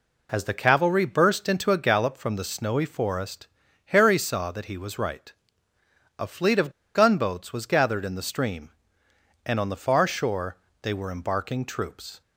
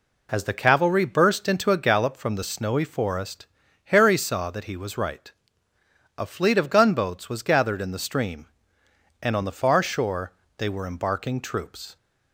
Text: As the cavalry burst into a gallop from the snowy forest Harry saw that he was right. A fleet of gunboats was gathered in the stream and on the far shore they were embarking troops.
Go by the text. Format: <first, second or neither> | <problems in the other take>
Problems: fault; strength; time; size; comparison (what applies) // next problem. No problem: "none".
second | pauses between "forest" and "Harry"; at 3.4 s; 0.38 s long; also in the second // pauses between "of" and "gunboats"; slight; at 6.7 s; 0.24 s long // pauses between "shore" and "they"; slight; at 10.5 s; 0.26 s long; slight in the second